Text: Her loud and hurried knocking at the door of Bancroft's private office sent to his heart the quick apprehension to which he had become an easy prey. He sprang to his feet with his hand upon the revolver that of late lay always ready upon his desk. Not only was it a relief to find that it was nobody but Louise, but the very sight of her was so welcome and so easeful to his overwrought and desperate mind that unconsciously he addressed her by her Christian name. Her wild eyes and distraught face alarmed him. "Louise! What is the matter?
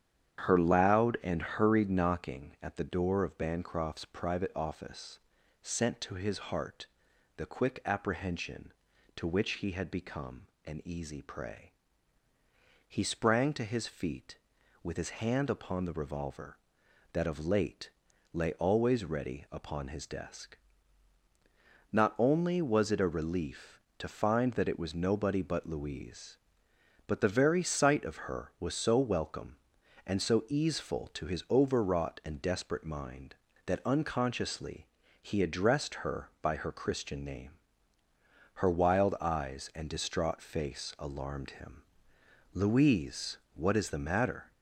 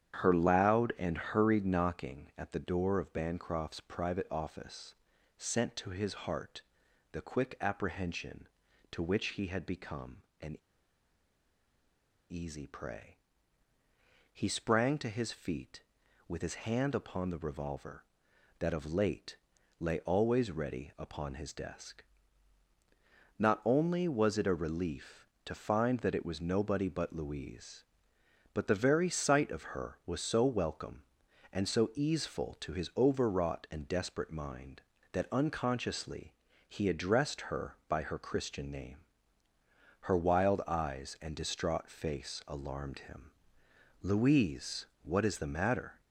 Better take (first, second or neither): first